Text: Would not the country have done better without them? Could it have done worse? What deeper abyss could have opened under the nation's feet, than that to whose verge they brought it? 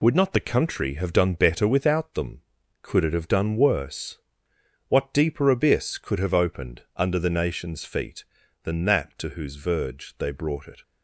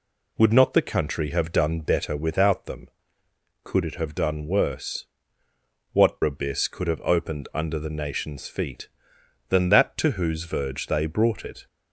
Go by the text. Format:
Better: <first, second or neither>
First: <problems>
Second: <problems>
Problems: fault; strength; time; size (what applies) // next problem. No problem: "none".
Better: first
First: none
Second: skips "deeper"; at 6.2 s